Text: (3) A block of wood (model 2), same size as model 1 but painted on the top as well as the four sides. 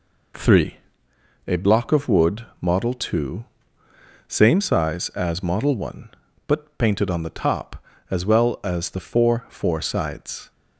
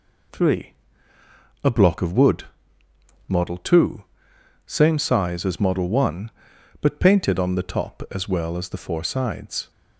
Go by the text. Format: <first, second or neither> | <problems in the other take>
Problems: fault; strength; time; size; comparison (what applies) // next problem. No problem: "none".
second | says "four" twice; at 9.4 s